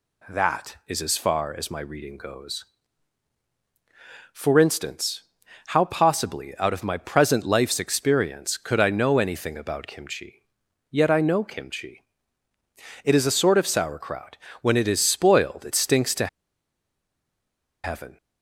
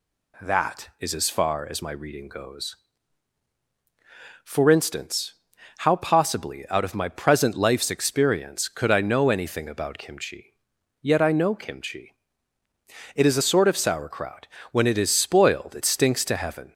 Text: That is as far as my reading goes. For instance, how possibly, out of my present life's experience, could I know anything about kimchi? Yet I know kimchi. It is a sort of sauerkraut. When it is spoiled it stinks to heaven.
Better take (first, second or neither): second